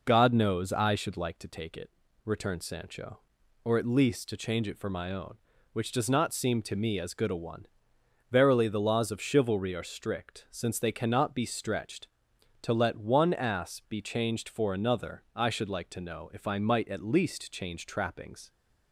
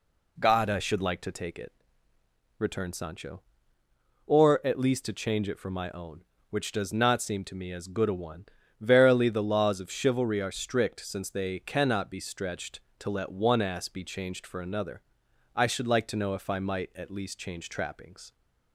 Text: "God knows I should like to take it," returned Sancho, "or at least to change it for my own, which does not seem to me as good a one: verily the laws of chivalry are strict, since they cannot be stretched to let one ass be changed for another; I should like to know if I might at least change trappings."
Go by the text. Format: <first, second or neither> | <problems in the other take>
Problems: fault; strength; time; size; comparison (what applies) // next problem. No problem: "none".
first | skips "knows"; at 0.6 s